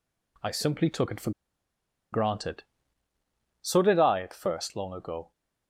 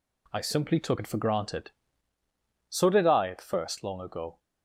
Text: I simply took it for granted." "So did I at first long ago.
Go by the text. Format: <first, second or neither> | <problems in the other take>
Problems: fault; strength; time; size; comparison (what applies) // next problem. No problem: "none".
second | pauses between "for" and "granted"; noticeable; at 1.3 s; 0.81 s long